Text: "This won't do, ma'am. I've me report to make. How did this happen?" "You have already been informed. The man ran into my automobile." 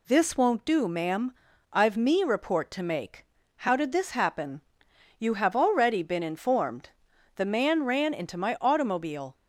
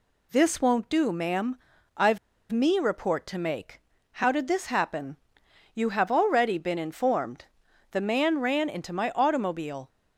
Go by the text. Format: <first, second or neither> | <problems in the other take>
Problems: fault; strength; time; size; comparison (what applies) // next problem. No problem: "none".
first | pauses between "I've" and "me"; slight; at 2.1 s; 0.34 s long